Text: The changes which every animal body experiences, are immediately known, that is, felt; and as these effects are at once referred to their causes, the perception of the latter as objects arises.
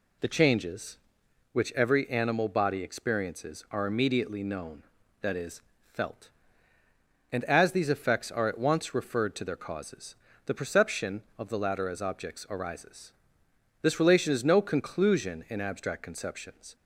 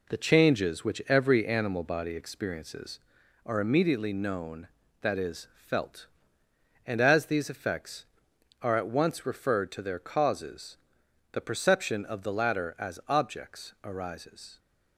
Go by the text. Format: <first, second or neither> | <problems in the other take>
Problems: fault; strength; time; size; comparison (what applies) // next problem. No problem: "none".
second | goes on to say "This relation is no conclusion in abstract conceptions"; strong; from 13.8 s on; 2.9 s long